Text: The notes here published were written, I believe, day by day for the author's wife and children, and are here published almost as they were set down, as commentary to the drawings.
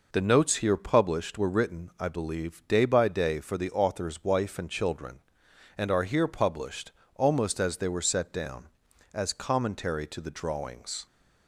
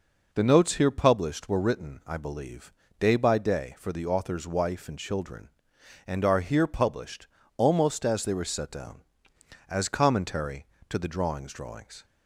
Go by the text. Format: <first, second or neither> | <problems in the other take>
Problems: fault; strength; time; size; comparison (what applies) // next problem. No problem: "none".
first | pauses between "published" and "almost"; slight; at 7.2 s; 0.30 s long; slight in the first // says "drawings" twice; at 11.5 s